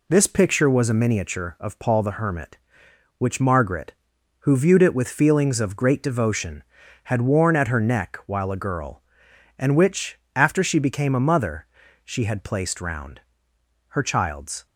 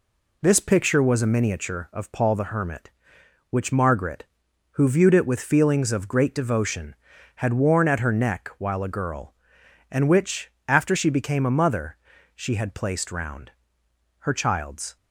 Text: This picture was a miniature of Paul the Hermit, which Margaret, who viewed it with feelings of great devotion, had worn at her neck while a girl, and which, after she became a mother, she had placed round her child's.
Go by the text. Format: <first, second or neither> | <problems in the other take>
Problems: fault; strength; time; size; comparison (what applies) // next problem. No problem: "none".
neither | pauses between "round" and "her"; noticeable; the same in both